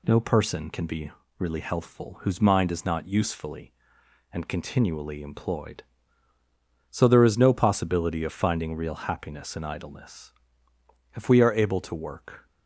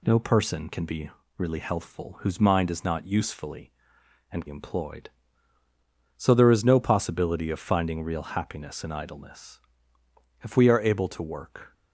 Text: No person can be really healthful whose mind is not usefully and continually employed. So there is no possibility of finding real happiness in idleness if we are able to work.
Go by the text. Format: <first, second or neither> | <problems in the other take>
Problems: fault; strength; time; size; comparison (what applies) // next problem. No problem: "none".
first | pauses between "be" and "really"; slight; at 1.0 s; 0.28 s long; slight in the first // skips "continually"; at 4.4 s // pauses between "idleness" and "if"; noticeable; at 9.5 s; 0.84 s long; noticeable in the first